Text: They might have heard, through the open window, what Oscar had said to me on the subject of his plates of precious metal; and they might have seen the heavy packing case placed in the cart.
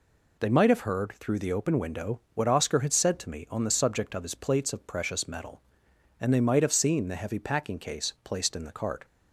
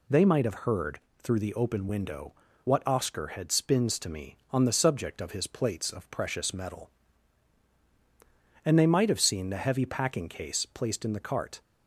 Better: first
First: none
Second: says "spins" for "said"; at 3.5 s

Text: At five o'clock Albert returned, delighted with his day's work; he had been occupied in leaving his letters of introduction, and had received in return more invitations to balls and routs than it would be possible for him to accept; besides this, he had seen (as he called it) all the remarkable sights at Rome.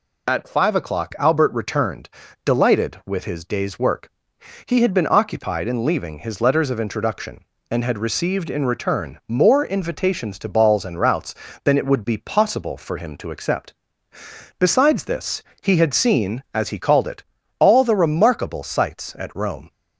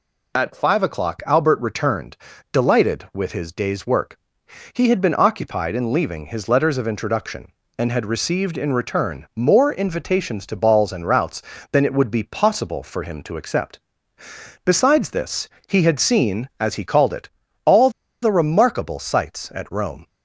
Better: first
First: none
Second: pauses between "all" and "the"; slight; at 17.8 s; 0.33 s long

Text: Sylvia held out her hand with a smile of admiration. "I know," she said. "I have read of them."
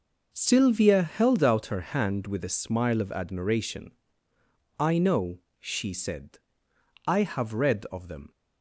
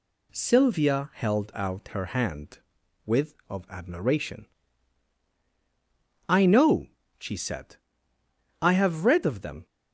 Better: first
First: none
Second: skips "a smile"; at 3.4 s

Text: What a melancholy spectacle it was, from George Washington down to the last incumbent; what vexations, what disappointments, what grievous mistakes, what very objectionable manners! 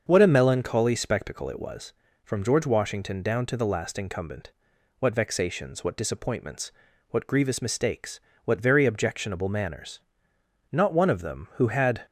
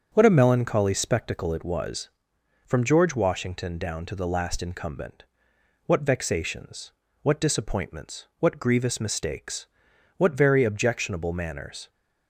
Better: second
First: starts louder than the rest; until 1.0 s; 6.5 dB // goes on to say "Not one of them who had"; from 10.7 s on; 1.3 s long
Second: starts louder than the rest; until 1.1 s; 6.5 dB

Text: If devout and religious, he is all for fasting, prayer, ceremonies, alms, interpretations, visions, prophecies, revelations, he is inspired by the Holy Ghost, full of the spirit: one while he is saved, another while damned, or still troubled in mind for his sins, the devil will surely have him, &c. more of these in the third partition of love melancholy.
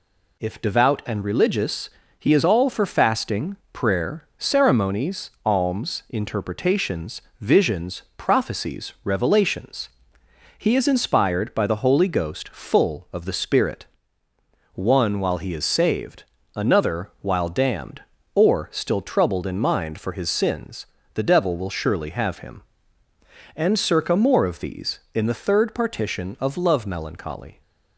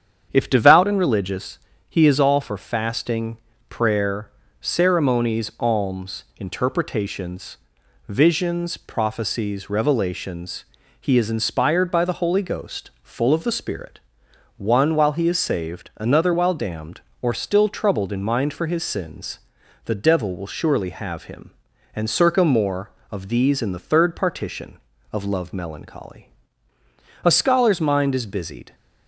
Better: first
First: none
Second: starts louder than the rest; strong; until 1.3 s; 8 dB // goes on to say "A scholar's mind is busied"; from 27.2 s on; 1.5 s long

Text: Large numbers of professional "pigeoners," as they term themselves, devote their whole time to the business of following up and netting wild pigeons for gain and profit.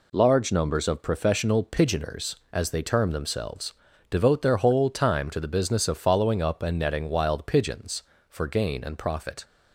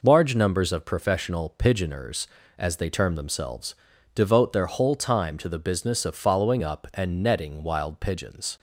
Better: first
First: none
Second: stops before "for gain and profit"; at 8.5 s

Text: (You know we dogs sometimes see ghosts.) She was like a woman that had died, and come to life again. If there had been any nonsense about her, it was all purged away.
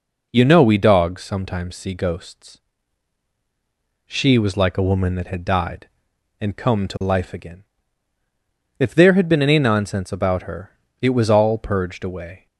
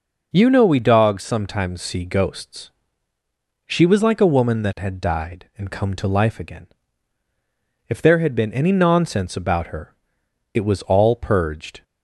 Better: first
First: none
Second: stops before "away"; at 11.8 s

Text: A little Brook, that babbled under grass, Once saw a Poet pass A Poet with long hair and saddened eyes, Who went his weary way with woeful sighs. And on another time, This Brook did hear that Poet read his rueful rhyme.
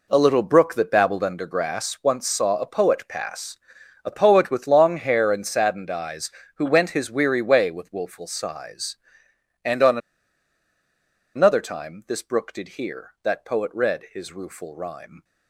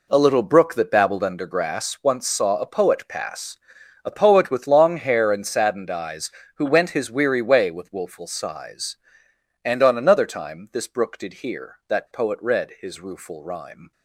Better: second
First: pauses between "pass" and "A"; noticeable; at 3.5 s; 0.46 s long // pauses between "on" and "another"; strong; at 9.9 s; 1.3 s long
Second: pauses between "pass" and "A"; noticeable; at 3.5 s; 0.46 s long

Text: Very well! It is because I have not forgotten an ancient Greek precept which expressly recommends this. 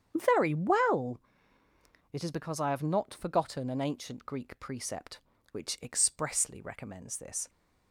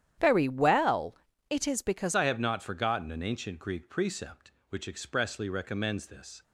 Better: first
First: starts louder than the rest; strong; until 1.1 s; 8.5 dB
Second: starts louder than the rest; strong; until 1.5 s; 10.5 dB // changes voice at "I"; from 2.1 s on; 4.3 s long

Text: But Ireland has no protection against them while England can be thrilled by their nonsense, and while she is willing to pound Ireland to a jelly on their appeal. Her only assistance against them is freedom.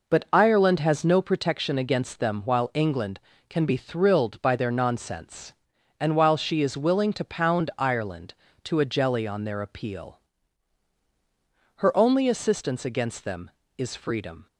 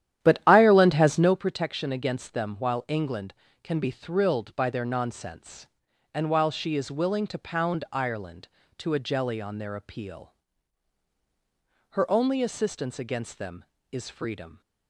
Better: first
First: none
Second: starts louder than the rest; strong; until 1.4 s; 11.5 dB

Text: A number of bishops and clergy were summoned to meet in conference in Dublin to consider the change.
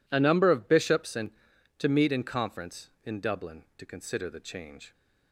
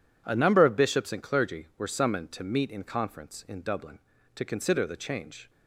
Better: second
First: skips "clergy were summoned"; at 1.5 s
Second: none

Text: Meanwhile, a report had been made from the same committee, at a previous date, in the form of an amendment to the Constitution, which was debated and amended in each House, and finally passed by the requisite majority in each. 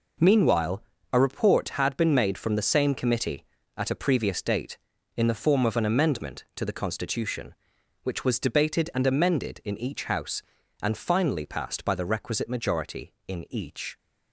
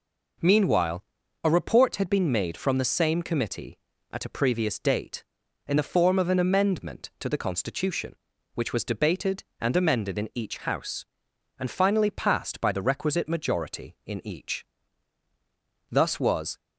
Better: first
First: none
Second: goes on to say "Thus was"; noticeable; from 15.9 s on; 0.68 s long

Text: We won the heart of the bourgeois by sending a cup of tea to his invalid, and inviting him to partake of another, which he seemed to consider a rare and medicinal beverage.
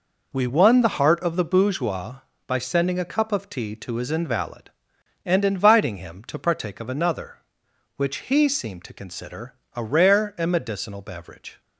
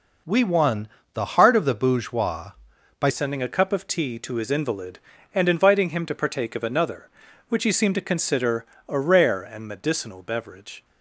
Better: first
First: pauses between "consider" and "a"; slight; at 9.5 s; 0.20 s long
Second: pauses between "won" and "the"; slight; at 0.8 s; 0.26 s long // changes voice at "sending"; from 3.0 s on; 7.8 s long // pauses between "consider" and "a"; slight; at 8.6 s; 0.24 s long

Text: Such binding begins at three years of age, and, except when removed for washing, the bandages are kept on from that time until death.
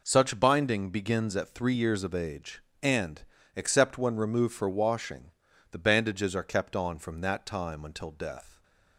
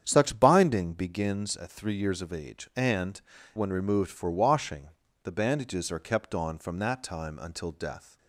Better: first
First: none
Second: starts louder than the rest; strong; until 1.0 s; 8.5 dB // skips "except"; at 3.3 s

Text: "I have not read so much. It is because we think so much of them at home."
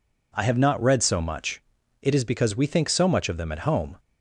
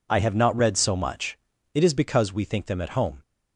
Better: first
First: none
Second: skips "so much of"; at 2.6 s

